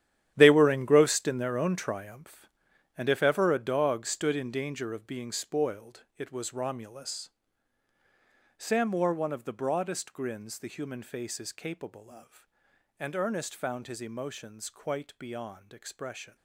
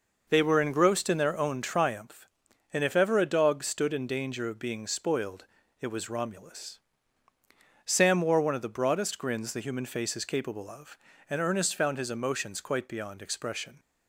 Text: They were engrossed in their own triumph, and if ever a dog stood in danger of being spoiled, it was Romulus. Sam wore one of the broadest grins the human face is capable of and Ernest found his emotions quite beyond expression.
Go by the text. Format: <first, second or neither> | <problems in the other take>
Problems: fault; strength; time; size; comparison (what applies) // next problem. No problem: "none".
second | gets quieter; strong; throughout; 13 dB